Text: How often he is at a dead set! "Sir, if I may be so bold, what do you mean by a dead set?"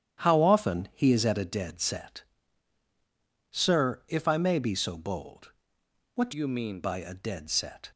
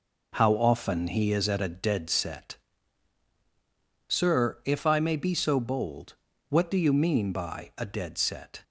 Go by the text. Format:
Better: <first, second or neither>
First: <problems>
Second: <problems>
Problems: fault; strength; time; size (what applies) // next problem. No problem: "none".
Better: second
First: starts louder than the rest; strong; until 1.2 s; 10.5 dB // changes voice from "you" to "mean"; from 6.3 to 6.8 s; 0.5 s long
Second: none